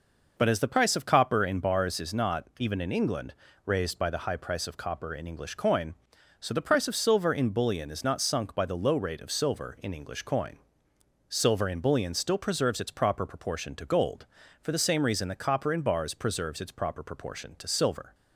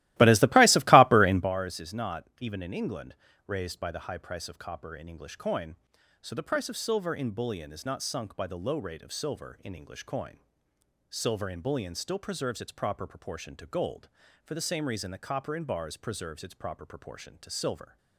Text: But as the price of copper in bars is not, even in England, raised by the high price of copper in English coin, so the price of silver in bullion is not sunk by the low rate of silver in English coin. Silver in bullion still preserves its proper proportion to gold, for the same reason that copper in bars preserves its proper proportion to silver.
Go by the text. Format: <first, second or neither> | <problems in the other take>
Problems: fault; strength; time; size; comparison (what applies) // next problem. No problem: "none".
first | starts louder than the rest; strong; until 1.5 s; 17.5 dB